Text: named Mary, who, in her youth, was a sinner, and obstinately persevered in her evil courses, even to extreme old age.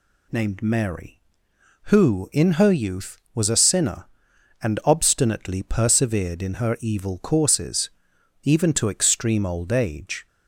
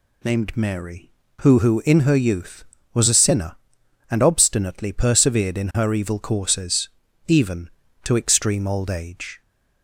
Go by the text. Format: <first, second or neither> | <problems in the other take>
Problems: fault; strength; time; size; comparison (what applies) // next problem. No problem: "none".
first | says "who" twice; at 1.5 s